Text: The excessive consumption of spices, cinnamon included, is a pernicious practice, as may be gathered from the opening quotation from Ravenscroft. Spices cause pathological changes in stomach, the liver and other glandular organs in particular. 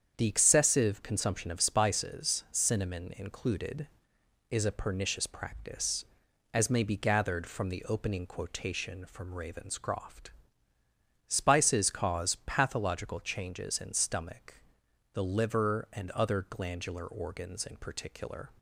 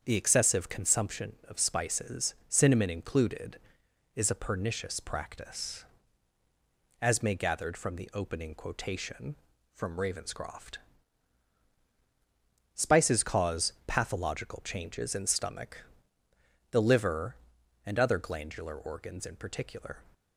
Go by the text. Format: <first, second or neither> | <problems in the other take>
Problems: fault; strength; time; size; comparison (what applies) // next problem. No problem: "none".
first | starts louder than the rest; strong; until 1.0 s; 7.5 dB; strong in the first // skips "be"; at 7.3 s